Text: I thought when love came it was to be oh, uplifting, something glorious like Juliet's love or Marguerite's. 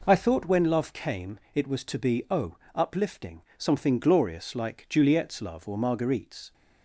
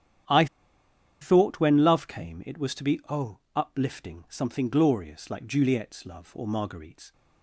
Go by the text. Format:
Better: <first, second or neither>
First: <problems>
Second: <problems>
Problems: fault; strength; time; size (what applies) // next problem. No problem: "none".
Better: first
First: none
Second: starts louder than the rest; strong; until 2.0 s; 10 dB // pauses between "I" and "thought"; noticeable; at 0.4 s; 0.75 s long